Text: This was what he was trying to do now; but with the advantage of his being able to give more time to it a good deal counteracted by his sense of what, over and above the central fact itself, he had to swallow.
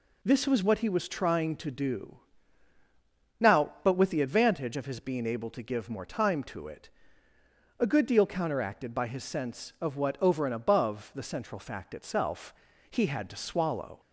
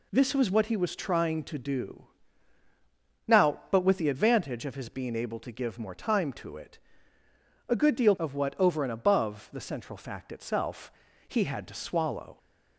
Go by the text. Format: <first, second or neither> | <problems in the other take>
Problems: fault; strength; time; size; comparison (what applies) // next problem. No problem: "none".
first | pauses between "do" and "now"; at 2.0 s; 1.2 s long; also in the first // pauses between "it" and "a"; noticeable; at 6.7 s; 0.88 s long; noticeable in the first // skips "counteracted by his sense"; at 8.1 s